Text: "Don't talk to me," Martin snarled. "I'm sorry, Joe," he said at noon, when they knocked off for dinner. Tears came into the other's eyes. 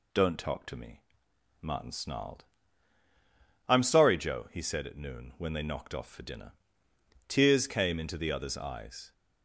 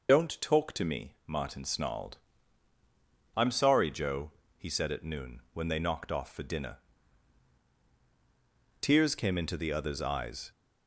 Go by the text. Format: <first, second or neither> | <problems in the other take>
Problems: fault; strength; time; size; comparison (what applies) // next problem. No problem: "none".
first | loses the start of "Don't"; at 0.0 s; 50 ms